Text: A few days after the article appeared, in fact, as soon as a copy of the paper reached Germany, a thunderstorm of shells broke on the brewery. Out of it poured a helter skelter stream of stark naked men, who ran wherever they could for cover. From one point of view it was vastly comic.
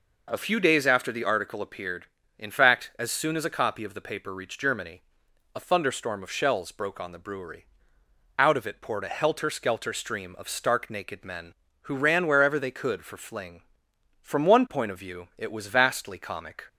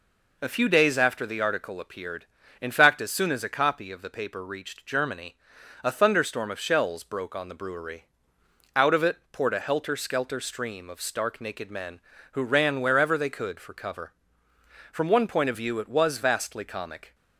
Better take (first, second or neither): second